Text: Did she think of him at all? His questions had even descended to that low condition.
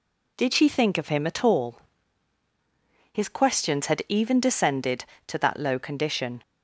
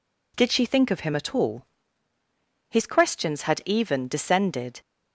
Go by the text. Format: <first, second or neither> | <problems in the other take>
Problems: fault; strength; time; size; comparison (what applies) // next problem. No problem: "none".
first | stops before "to that low condition"; at 4.8 s